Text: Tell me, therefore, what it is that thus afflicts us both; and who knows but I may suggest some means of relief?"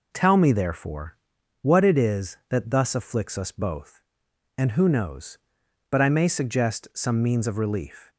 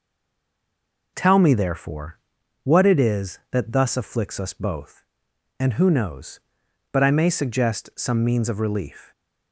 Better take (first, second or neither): first